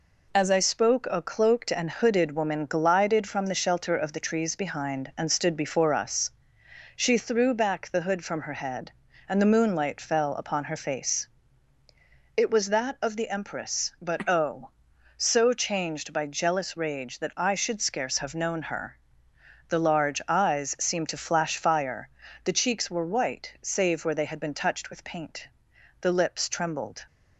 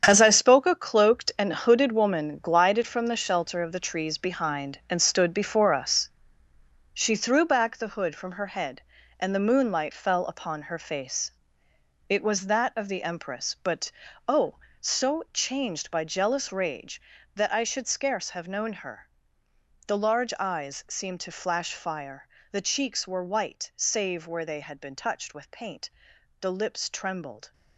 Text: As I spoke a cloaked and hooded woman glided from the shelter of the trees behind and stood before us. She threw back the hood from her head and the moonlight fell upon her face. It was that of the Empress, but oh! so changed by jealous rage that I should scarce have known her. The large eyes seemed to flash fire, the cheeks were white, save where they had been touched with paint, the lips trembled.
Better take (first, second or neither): first